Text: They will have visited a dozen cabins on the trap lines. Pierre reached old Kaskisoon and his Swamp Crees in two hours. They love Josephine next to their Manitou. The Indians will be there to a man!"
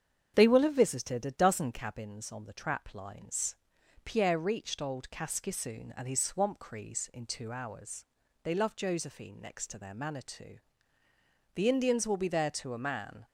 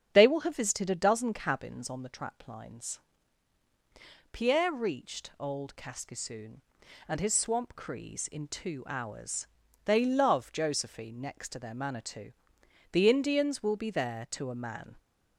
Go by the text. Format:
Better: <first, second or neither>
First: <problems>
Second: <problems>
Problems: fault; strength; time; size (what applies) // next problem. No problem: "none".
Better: neither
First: starts louder than the rest; strong; until 1.3 s; 8 dB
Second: starts louder than the rest; strong; until 1.1 s; 8 dB